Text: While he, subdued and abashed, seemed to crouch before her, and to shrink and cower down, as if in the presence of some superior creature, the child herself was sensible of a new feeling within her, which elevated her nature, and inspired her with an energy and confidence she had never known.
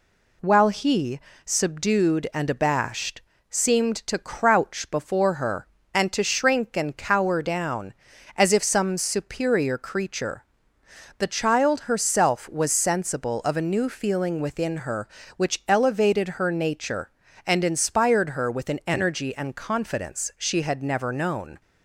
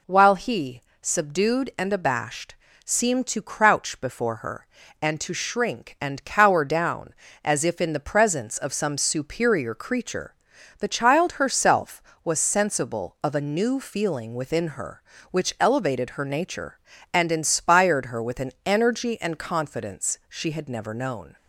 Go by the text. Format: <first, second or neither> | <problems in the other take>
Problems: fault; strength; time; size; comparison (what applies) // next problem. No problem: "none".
second | skips "in the presence of"; at 8.6 s